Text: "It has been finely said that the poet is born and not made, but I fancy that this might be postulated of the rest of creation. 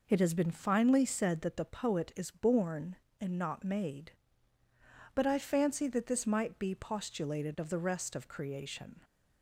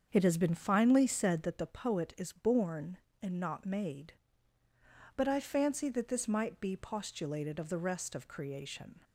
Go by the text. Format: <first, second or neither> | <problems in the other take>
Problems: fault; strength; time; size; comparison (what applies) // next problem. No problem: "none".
first | starts louder than the rest; until 1.6 s; 7 dB